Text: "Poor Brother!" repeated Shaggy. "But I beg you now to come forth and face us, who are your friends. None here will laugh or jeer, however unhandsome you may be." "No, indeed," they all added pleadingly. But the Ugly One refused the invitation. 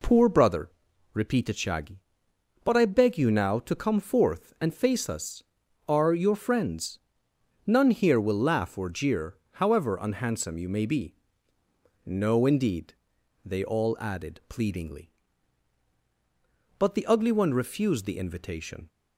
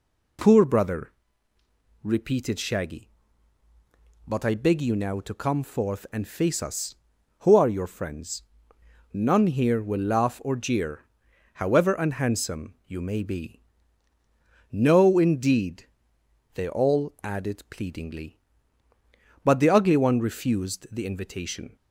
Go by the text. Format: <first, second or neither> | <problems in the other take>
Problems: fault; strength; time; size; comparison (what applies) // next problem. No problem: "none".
second | skips "who"; at 5.6 s